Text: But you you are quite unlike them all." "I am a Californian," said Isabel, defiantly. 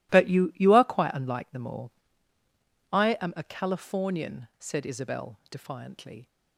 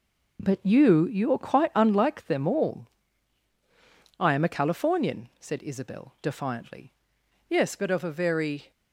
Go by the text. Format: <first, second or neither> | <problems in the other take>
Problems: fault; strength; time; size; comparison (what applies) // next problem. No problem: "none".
first | goes on to say "Yes but of a very"; noticeable; from 7.4 s on; 1.2 s long